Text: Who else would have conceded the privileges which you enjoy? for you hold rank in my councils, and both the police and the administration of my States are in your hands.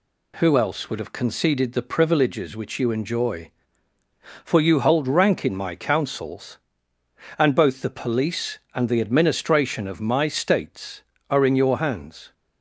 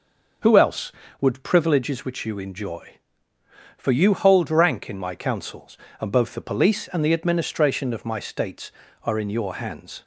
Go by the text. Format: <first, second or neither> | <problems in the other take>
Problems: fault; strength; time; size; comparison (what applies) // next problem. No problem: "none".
first | skips "have conceded the"; at 1.4 s